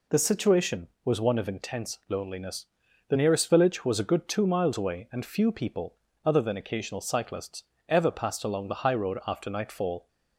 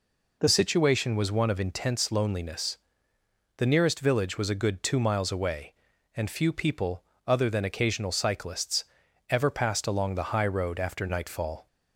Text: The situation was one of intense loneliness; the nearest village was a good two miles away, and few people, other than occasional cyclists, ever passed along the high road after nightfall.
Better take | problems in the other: first | changes voice at "situation"; from 0.4 s on; 11.2 s long

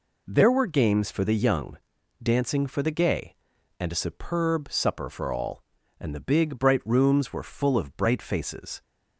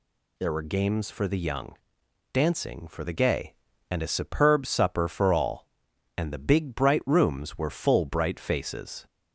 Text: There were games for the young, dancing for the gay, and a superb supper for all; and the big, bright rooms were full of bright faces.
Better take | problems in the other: first | skips "of"; at 8.0 s

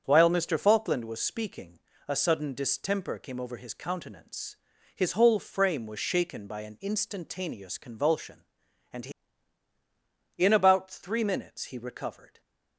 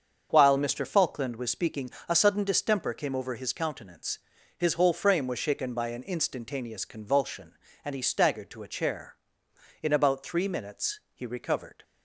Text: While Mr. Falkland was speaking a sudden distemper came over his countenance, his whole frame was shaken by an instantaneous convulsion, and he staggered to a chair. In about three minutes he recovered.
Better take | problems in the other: second | starts louder than the rest; strong; until 1.0 s; 7.5 dB; also in the second // pauses between "speaking" and "a"; slight; at 1.7 s; 0.28 s long; slight in the second // skips "staggered to a chair"; at 9.7 s

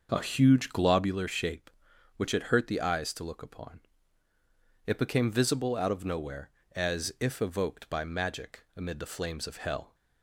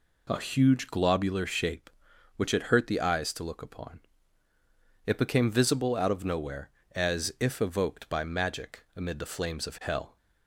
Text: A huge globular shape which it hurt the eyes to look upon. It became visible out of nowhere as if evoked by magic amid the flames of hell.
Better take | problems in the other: second | starts louder than the rest; noticeable; until 1.2 s; 6 dB

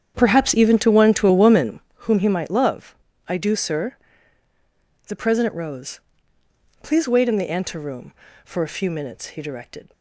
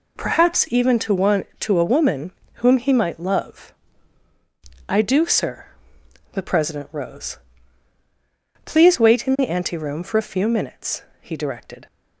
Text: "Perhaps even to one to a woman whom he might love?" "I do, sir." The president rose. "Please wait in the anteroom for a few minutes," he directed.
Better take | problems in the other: second | starts louder than the rest; strong; until 2.0 s; 8.5 dB // pauses between "woman" and "whom"; slight; at 1.8 s; 0.26 s long; slight in the second

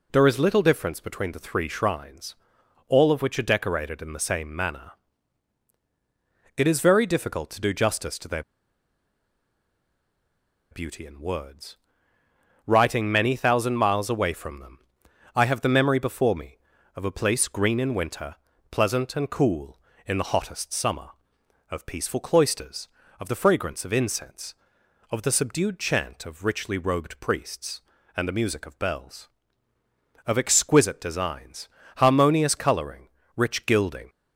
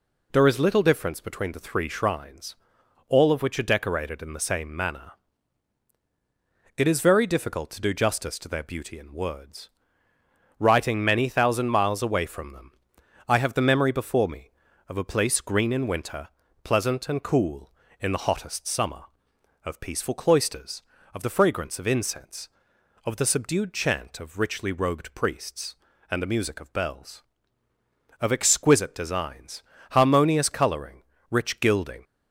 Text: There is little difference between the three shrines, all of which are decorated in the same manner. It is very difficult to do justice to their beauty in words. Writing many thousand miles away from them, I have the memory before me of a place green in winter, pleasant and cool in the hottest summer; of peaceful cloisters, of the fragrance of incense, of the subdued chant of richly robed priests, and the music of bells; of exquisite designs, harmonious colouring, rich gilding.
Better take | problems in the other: second | pauses between "their" and "beauty"; strong; at 8.4 s; 2.2 s long

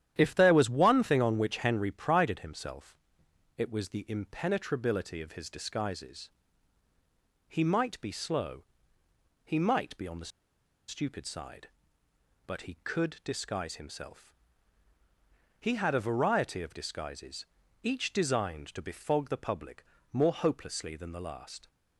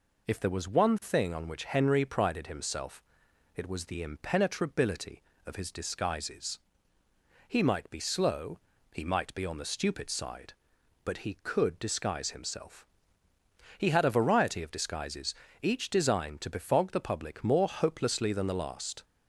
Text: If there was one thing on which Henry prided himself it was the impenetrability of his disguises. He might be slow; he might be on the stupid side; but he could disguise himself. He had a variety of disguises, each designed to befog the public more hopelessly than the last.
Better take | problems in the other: second | starts louder than the rest; strong; until 1.1 s; 10.5 dB // pauses between "himself" and "it"; noticeable; at 2.9 s; 0.62 s long; noticeable in the second // pauses between "the" and "stupid"; noticeable; at 10.3 s; 0.58 s long // pauses between "public" and "more"; slight; at 19.8 s; 0.26 s long

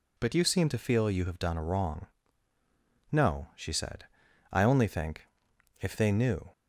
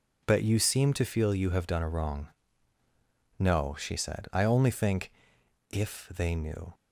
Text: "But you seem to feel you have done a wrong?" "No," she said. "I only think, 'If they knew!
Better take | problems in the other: neither | none

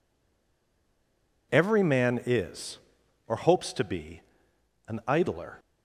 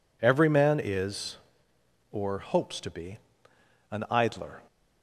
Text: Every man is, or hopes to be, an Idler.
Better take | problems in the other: second | stays silent before the first word; noticeable; until 1.5 s; 1.5 s long

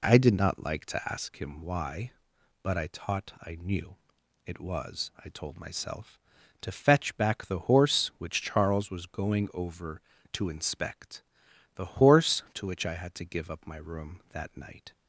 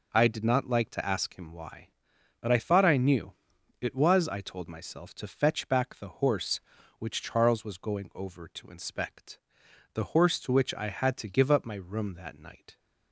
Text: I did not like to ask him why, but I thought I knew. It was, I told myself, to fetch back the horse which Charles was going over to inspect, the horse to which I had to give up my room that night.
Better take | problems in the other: second | says "taught" for "thought"; at 2.9 s

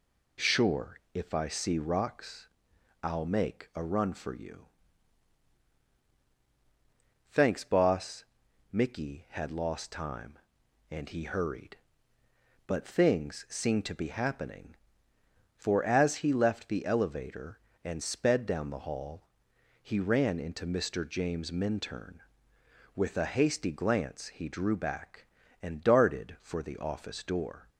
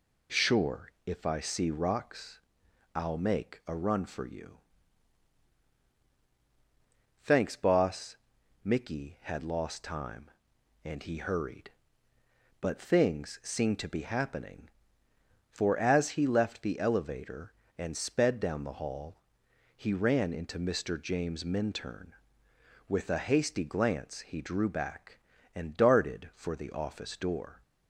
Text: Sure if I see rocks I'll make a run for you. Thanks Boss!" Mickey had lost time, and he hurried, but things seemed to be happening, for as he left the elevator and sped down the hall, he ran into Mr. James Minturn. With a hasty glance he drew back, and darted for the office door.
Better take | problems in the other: neither | pauses between "rocks" and "I'll"; noticeable; the same in both

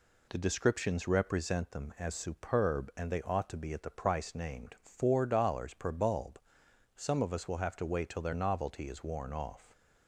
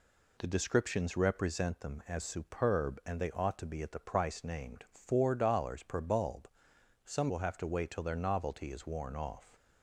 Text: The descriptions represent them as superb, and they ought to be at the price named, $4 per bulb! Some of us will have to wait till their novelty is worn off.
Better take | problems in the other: first | skips "of us"; at 7.2 s

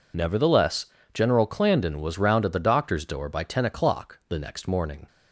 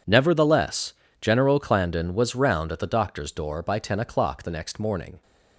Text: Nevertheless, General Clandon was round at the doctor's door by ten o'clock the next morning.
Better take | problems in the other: second | loses the start of "Nevertheless"; at 0.1 s; 40 ms

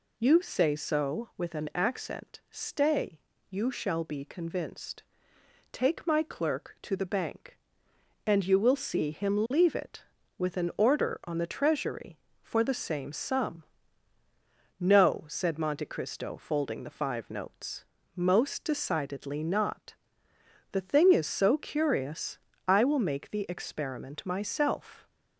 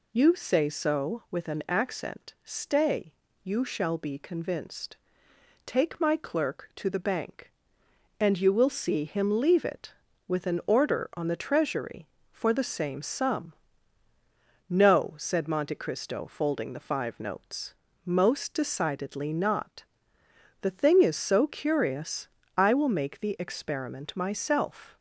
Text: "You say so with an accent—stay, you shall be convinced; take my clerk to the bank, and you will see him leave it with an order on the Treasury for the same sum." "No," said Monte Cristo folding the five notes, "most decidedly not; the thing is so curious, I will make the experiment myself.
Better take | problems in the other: neither | none

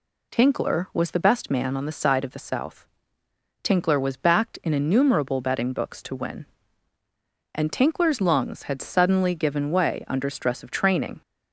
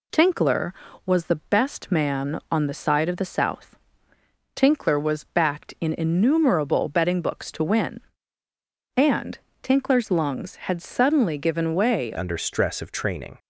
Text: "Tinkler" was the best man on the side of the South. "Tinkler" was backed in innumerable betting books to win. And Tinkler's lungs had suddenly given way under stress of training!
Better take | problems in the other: first | pauses between "And" and "Tinkler's"; slight; at 9.3 s; 0.24 s long // changes voice at "under"; from 12.1 s on; 1.2 s long

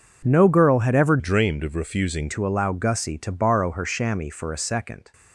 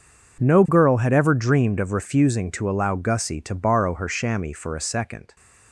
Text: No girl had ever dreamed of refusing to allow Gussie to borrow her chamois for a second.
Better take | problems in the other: second | changes voice from "dreamed" to "refusing"; from 1.1 to 2.2 s; 1.1 s long

